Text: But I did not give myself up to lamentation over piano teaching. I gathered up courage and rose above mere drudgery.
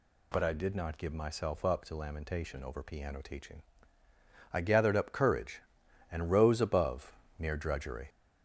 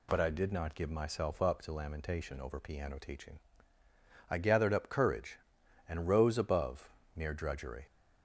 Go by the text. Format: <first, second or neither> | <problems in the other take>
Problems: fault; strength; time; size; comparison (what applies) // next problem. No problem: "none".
second | gets louder; noticeable; throughout; 5 dB // pauses between "above" and "mere"; slight; at 7.1 s; 0.26 s long; slight in the second